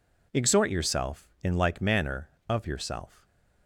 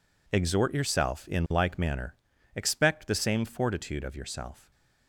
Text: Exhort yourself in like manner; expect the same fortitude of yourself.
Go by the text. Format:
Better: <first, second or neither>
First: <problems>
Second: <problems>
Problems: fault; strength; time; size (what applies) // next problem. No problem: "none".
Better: second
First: skips "expect the same fortitude"; at 2.3 s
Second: none